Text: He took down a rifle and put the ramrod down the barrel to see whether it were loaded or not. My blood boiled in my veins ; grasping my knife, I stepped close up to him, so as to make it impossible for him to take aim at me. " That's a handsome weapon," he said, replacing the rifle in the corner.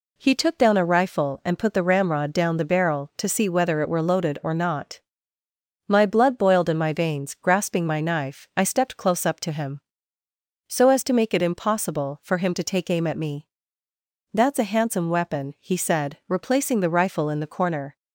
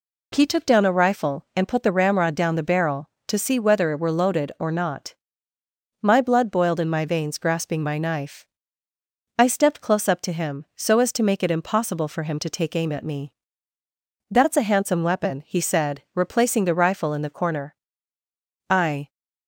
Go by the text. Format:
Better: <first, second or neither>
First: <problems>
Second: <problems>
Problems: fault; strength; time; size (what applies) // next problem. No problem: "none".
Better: first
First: none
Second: goes on to say "I"; slight; from 18.7 s on; 0.38 s long